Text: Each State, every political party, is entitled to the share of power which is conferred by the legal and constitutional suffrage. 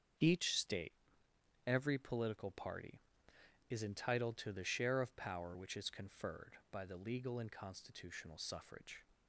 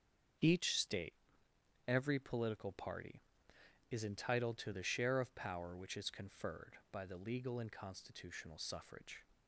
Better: neither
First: starts louder than the rest; until 1.9 s; 7 dB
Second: starts louder than the rest; until 2.1 s; 7 dB

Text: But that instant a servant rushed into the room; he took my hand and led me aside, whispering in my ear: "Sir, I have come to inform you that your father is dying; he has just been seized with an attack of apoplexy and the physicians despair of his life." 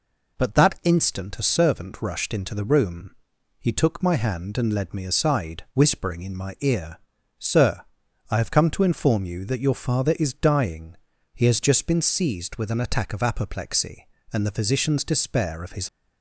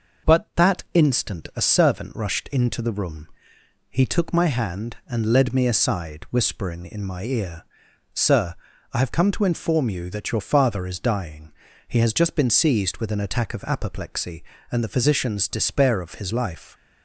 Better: second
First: stops before "life"; at 15.8 s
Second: none

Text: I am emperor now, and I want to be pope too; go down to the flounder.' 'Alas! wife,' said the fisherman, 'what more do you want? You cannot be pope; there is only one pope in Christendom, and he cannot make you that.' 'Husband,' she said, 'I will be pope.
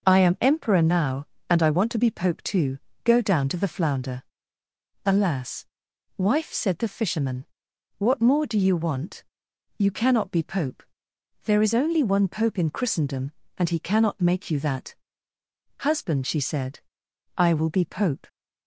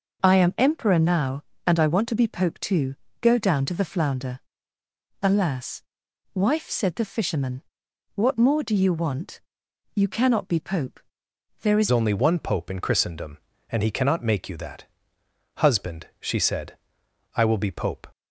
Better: first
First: none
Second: changes voice at "only"; from 11.8 s on; 6.2 s long

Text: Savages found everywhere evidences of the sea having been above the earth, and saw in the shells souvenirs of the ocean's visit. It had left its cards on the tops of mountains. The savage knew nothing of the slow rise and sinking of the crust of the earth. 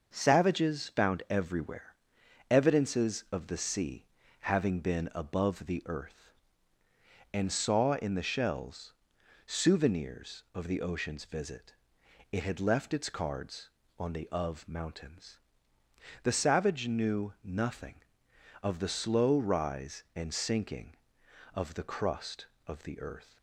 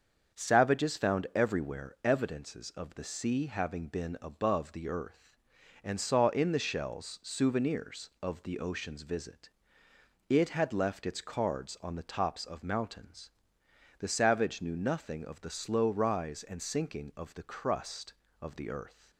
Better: second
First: starts louder than the rest; until 1.1 s; 6 dB // pauses between "everywhere" and "evidences"; noticeable; at 1.9 s; 0.56 s long // pauses between "sea" and "having"; at 4.0 s; 0.36 s long // pauses between "shells" and "souvenirs"; noticeable; at 8.9 s; 0.54 s long // skips "tops"; at 14.2 s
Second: starts louder than the rest; until 1.4 s; 7 dB

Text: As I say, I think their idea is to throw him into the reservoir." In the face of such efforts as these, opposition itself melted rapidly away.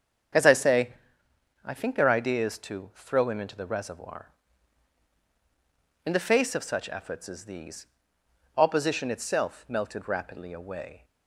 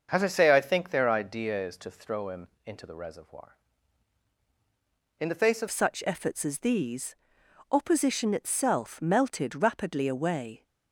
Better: first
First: starts louder than the rest; strong; until 2.0 s; 7.5 dB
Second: starts louder than the rest; until 1.1 s; 6.5 dB // pauses between "him" and "into"; slight; at 2.4 s; 0.18 s long // changes voice at "such"; from 5.6 s on; 5.0 s long

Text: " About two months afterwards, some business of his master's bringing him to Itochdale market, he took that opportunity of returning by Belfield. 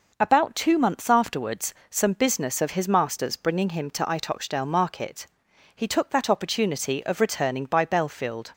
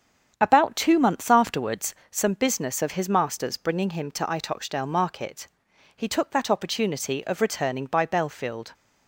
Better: first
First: none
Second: starts louder than the rest; strong; until 1.9 s; 8 dB

